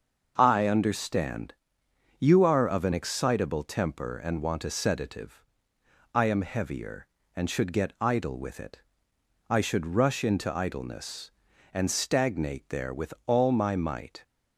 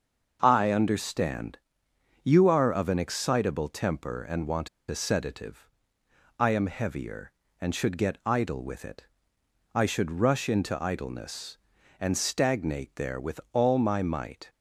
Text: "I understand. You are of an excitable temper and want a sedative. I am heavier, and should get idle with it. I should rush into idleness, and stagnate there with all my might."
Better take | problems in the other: first | starts louder than the rest; until 1.4 s; 6.5 dB; also in the first // pauses between "want" and "a"; slight; at 4.6 s; 0.21 s long

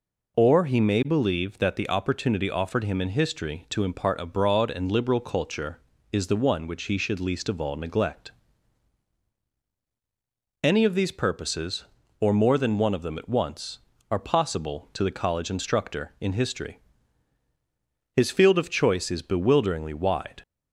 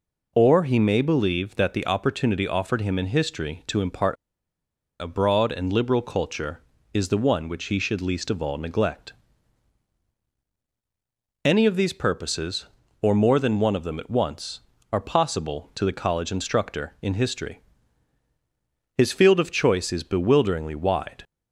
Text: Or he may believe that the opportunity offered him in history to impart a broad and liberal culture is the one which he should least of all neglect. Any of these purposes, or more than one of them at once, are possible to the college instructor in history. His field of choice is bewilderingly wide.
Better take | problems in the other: first | pauses between "impart" and "a"; noticeable; at 4.1 s; 0.85 s long

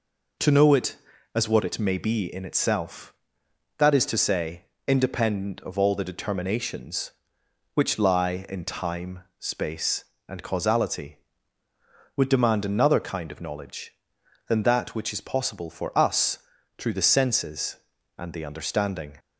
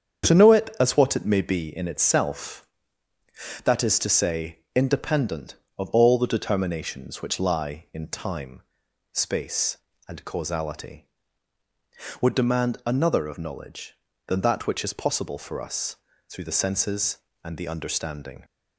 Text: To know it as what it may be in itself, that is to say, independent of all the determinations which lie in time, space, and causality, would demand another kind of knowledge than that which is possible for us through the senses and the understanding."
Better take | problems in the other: first | starts louder than the rest; strong; until 1.3 s; 7.5 dB // skips "kind"; at 13.2 s // pauses between "us" and "through"; slight; at 15.9 s; 0.34 s long; also in the first

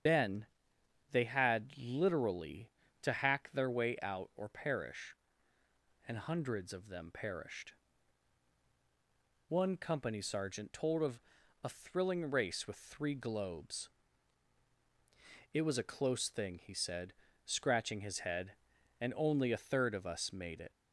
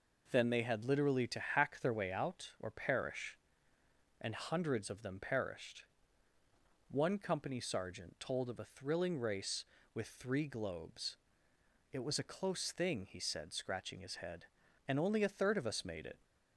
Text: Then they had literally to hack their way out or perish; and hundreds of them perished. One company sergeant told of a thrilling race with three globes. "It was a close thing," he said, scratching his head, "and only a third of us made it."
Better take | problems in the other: second | loses the start of "Then"; at 0.0 s; 40 ms // starts louder than the rest; strong; until 1.7 s; 7.5 dB // pauses between "Then" and "they"; noticeable; at 0.4 s; 0.66 s long // pauses between "of" and "a"; at 11.1 s; 0.44 s long

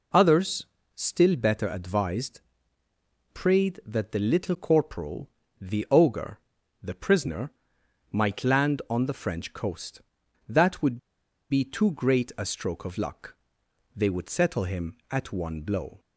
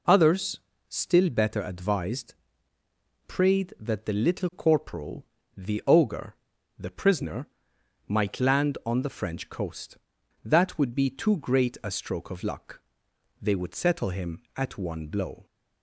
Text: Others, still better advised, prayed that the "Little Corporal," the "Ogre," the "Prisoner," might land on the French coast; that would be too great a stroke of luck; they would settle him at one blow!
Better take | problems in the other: second | pauses between "would" and "be"; noticeable; at 10.9 s; 0.53 s long

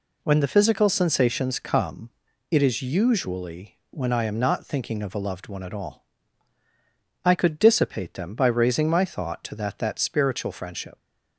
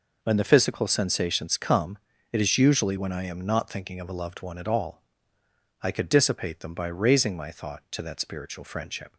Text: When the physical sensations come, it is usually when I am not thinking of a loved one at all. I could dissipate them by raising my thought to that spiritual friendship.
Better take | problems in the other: second | says "that" twice; at 9.7 s

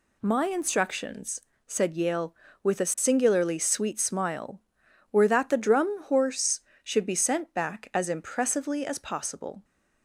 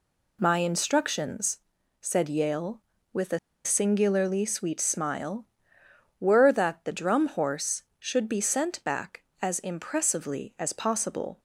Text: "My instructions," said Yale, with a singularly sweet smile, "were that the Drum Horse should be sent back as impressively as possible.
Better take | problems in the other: first | pauses between "a" and "singularly"; slight; at 3.3 s; 0.26 s long

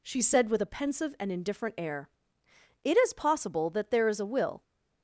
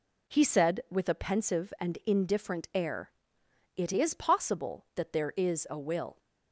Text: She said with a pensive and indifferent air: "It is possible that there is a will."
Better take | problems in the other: first | says "He" for "She"; at 0.2 s

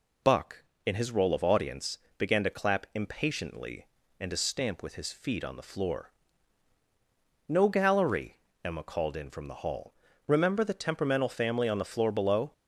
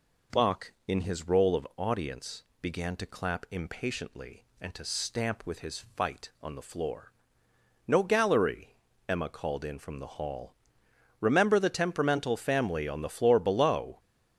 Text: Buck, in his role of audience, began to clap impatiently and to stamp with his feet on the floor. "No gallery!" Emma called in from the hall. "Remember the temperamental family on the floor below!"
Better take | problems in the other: first | says "fight" for "feet"; at 5.8 s

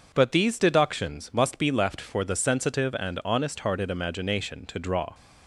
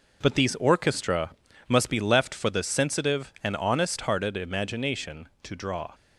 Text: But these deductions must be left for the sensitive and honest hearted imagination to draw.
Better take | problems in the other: first | says "orchestra" for "deductions"; at 0.5 s

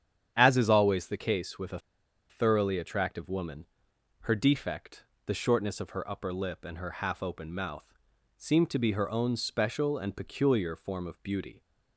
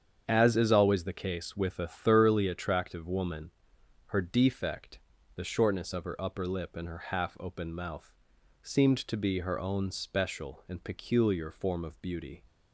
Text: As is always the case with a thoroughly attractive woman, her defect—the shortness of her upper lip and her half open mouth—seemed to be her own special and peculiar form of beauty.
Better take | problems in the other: second | starts louder than the rest; strong; until 1.3 s; 8.5 dB; strong in the second // pauses between "a" and "thoroughly"; noticeable; at 1.7 s; 0.51 s long

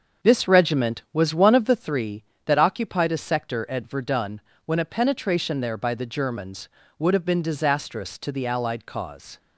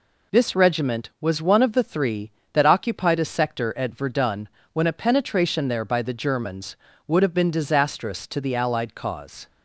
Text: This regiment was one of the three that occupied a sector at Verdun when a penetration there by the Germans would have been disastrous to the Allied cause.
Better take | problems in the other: second | starts louder than the rest; until 2.0 s; 6.5 dB // pauses between "Verdun" and "when"; slight; at 4.4 s; 0.24 s long; slight in the second

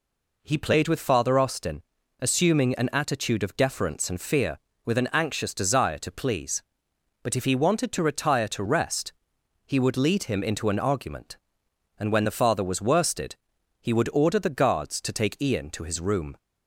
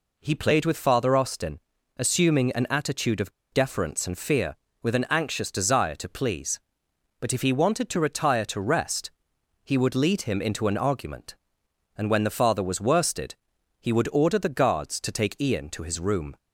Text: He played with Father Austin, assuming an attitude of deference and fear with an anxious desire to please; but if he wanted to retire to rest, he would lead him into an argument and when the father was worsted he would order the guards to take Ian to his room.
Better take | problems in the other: first | pauses between "of" and "deference"; slight; at 3.3 s; 0.21 s long // pauses between "worsted" and "he"; noticeable; at 13.3 s; 0.48 s long; noticeable in the first

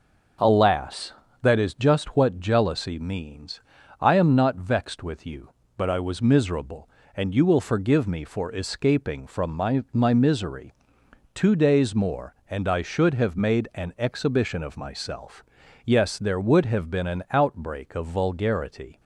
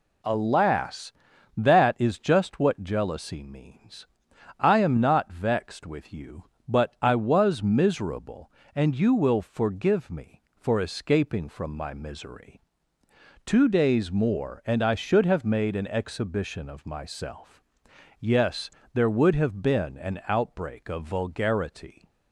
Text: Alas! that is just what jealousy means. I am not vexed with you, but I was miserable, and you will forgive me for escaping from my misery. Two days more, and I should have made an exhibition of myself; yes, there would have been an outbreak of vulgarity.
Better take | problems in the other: second | starts louder than the rest; noticeable; until 1.7 s; 6 dB // says "my" twice; at 9.9 s

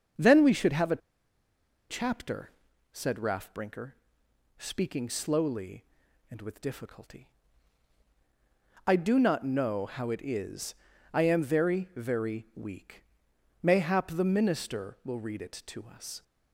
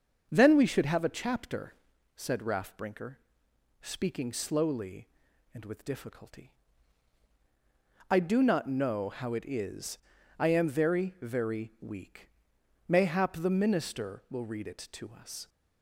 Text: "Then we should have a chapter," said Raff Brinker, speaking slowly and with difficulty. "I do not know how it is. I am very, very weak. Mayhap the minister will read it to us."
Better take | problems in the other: second | starts louder than the rest; until 2.0 s; 6.5 dB; also in the second // pauses between "a" and "chapter"; noticeable; at 1.0 s; 0.90 s long

